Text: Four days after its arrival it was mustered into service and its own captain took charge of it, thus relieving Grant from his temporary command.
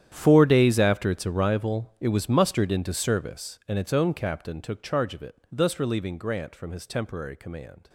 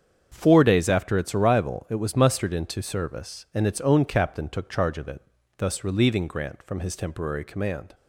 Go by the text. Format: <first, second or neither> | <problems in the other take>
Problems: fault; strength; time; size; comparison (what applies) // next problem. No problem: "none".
second | gets quieter; strong; throughout; 17 dB // starts louder than the rest; strong; until 1.1 s; 10.5 dB; strong in the second